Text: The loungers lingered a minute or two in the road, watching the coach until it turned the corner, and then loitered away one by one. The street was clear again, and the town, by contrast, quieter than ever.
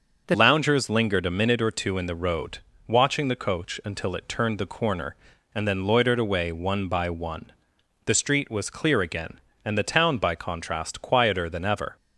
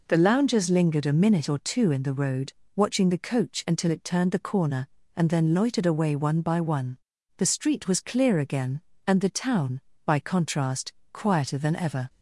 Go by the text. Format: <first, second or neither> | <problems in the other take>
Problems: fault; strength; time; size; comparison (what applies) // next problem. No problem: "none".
second | starts louder than the rest; until 1.2 s; 6.5 dB // changes voice at "loungers"; from 0.3 s on; 11.6 s long